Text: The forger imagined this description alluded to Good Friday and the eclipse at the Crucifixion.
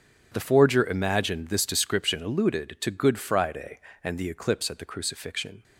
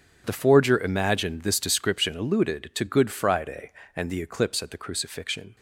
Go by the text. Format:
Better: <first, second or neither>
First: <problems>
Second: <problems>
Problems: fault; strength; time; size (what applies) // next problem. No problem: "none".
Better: neither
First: starts louder than the rest; until 1.3 s; 7 dB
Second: starts louder than the rest; until 1.2 s; 6.5 dB